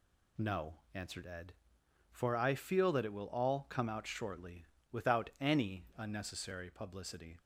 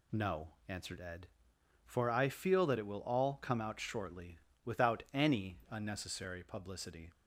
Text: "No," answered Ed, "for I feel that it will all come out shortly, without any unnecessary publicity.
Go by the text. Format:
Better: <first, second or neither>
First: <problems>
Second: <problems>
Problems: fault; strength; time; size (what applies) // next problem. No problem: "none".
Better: neither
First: none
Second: none